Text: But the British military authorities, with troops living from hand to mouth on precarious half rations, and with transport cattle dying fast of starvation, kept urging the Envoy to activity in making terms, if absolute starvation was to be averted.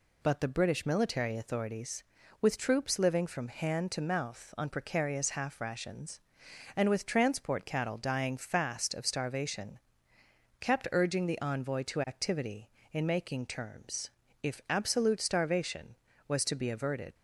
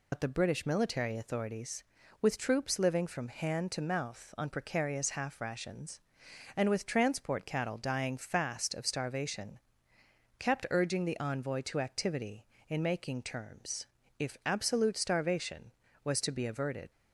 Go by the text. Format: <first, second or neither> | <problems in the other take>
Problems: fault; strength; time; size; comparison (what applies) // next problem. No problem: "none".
first | loses the start of "But"; at 0.1 s; 80 ms